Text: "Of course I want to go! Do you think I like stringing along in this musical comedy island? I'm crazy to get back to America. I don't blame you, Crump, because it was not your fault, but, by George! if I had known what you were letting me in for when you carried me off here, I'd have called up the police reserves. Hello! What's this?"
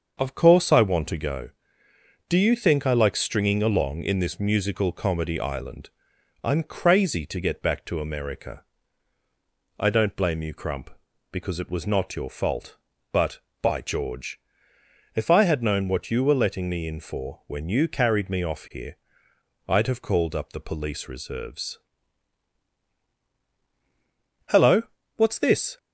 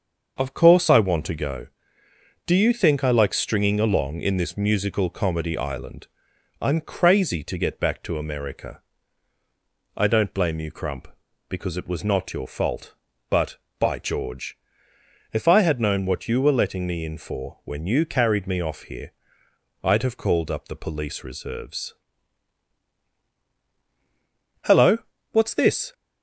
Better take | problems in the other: neither | starts louder than the rest; the same in both

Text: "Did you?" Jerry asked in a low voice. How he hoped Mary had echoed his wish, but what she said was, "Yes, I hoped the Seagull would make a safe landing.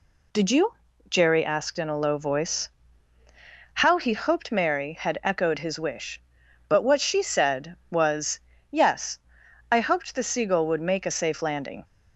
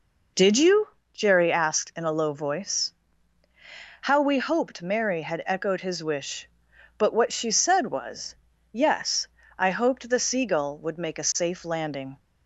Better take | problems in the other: first | says "we" for "he"; at 4.2 s

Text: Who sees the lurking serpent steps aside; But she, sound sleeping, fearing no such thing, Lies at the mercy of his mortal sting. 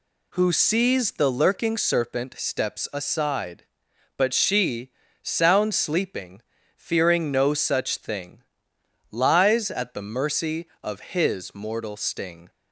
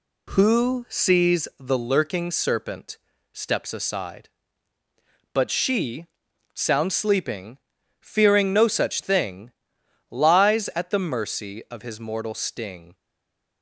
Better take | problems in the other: first | pauses between "serpent" and "steps"; slight; at 2.9 s; 0.34 s long // stays silent after the last word; slight; from 12.9 s on; 0.7 s long

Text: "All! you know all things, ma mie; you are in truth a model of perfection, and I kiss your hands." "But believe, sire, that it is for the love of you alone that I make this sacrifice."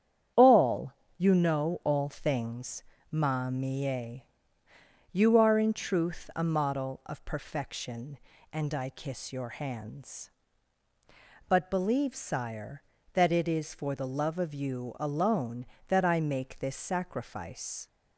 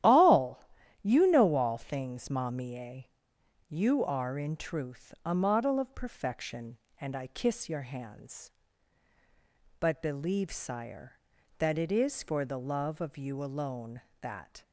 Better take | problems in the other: first | starts louder than the rest; strong; until 1.4 s; 12.5 dB; strong in the first // stops before "I make this sacrifice"; at 14.6 s

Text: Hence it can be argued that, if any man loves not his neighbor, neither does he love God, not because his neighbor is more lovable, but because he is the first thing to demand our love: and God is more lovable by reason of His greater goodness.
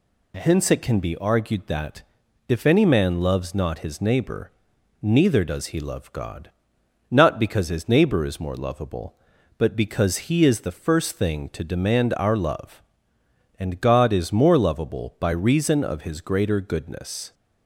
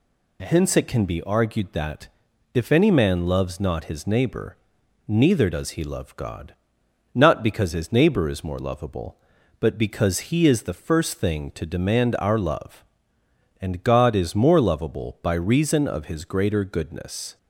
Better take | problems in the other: neither | none

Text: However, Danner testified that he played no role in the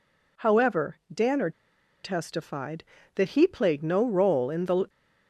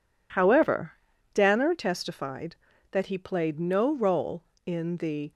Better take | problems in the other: second | pauses between "Danner" and "testified"; noticeable; at 1.5 s; 0.51 s long

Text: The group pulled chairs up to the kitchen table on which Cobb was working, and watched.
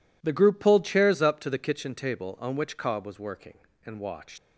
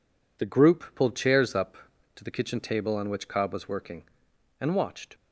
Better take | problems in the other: second | leaves "watched" unfinished; at 4.3 s; 125 ms

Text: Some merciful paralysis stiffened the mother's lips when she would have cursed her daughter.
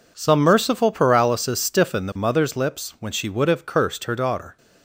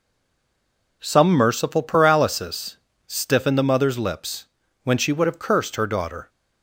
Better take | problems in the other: first | stays silent before the first word; until 1.0 s; 1.0 s long // pauses between "paralysis" and "stiffened"; slight; at 2.7 s; 0.30 s long // pauses between "lips" and "when"; at 4.4 s; 0.40 s long

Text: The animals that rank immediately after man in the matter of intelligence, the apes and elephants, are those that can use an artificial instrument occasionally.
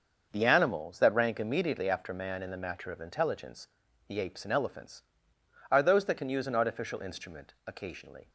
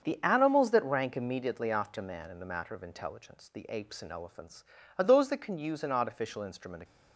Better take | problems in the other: first | starts louder than the rest; until 1.0 s; 7 dB; also in the first // stops before "occasionally"; at 6.8 s

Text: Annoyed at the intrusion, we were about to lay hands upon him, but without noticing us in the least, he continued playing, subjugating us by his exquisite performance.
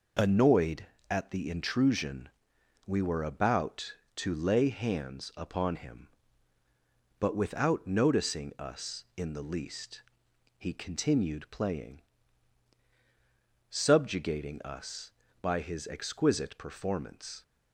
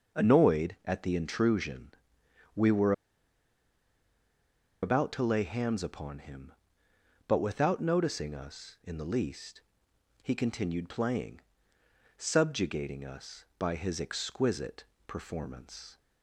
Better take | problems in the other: first | pauses between "were" and "about"; strong; at 2.9 s; 1.9 s long // pauses between "exquisite" and "performance"; slight; at 14.8 s; 0.24 s long

